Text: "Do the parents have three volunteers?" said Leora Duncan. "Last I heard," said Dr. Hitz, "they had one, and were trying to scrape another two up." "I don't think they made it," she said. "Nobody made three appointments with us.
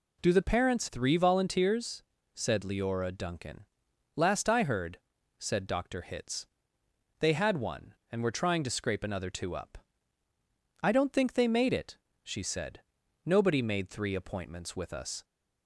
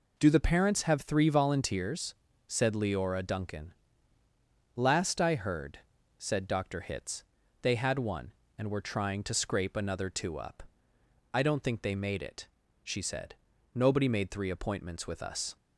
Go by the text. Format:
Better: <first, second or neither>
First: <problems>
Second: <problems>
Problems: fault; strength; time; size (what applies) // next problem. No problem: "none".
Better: second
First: skips "have"; at 0.8 s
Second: none